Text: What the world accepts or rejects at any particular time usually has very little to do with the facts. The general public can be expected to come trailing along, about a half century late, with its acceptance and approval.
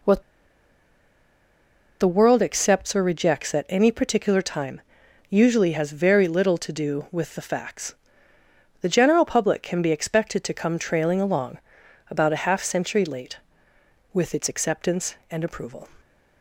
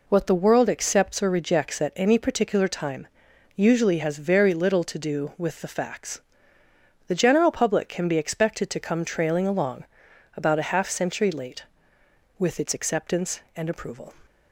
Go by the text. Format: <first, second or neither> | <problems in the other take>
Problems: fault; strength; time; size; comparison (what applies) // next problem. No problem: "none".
second | pauses between "What" and "the"; strong; at 0.2 s; 1.7 s long // pauses between "time" and "usually"; noticeable; at 4.8 s; 0.48 s long; noticeable in the second